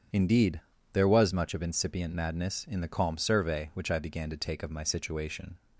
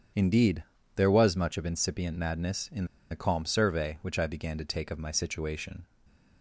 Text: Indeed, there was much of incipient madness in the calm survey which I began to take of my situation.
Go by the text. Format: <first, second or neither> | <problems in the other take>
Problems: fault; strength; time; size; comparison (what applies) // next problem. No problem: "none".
first | starts louder than the rest; strong; until 1.4 s; 8 dB; strong in the first // pauses between "in" and "the"; slight; at 2.8 s; 0.25 s long // stays silent after the last word; slight; from 5.8 s on; 0.6 s long